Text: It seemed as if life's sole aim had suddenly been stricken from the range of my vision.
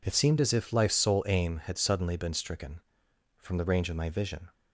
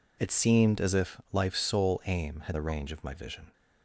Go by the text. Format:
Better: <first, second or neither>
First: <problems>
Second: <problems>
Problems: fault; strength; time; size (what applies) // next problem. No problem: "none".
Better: first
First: none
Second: skips "suddenly been stricken from"; at 2.5 s